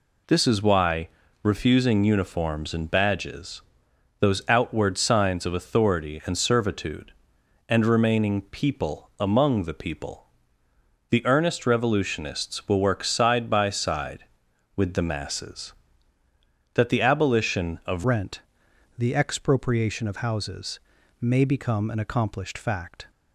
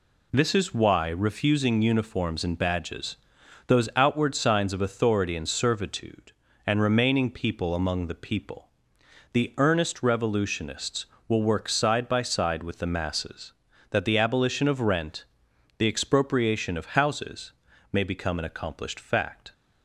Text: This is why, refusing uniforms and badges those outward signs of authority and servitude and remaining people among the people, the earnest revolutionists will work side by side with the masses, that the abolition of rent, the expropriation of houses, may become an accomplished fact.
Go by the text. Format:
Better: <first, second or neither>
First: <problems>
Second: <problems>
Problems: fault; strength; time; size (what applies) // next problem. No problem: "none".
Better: second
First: pauses between "badges" and "those"; noticeable; at 3.6 s; 0.58 s long // changes voice at "rent"; from 18.0 s on; 5.1 s long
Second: pauses between "badges" and "those"; noticeable; at 3.1 s; 0.50 s long